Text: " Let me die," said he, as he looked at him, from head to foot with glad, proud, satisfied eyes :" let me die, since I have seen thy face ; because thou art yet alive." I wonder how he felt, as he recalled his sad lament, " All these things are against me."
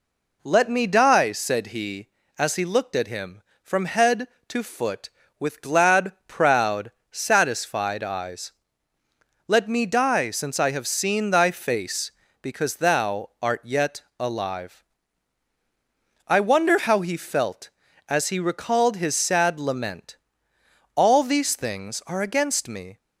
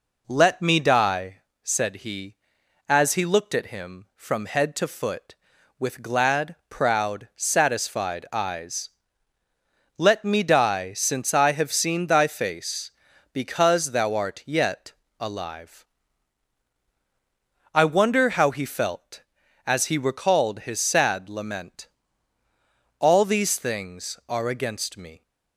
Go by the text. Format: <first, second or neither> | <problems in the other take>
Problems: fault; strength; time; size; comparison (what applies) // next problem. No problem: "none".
neither | pauses between "yet" and "alive"; slight; the same in both